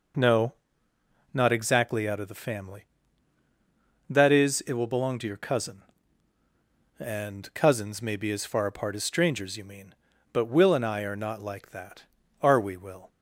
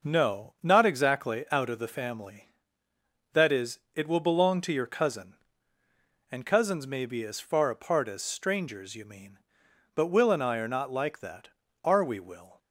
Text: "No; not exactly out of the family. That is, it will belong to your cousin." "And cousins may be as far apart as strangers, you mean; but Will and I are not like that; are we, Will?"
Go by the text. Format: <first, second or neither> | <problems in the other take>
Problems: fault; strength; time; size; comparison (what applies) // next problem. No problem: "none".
neither | none